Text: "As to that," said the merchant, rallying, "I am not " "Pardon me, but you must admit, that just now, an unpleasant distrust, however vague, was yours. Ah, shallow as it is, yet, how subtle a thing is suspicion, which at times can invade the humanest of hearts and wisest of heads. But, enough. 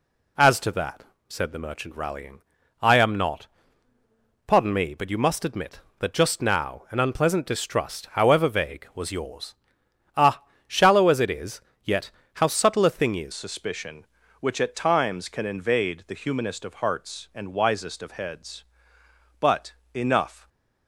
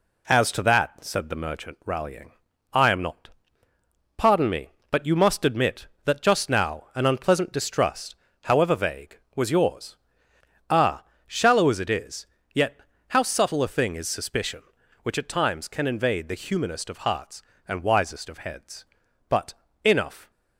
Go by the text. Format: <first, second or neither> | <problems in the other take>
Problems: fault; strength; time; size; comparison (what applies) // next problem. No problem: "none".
second | changes voice at "suspicion"; from 13.3 s on; 7.1 s long